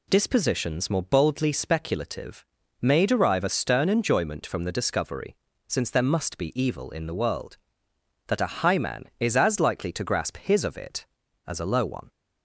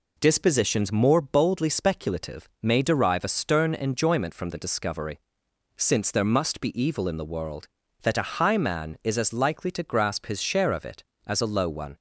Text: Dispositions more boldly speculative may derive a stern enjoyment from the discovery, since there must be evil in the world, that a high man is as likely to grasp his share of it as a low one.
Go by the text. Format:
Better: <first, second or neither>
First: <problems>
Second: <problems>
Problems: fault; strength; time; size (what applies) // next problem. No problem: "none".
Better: second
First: pauses between "speculative" and "may"; at 2.4 s; 0.38 s long // skips "share"; at 10.6 s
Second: none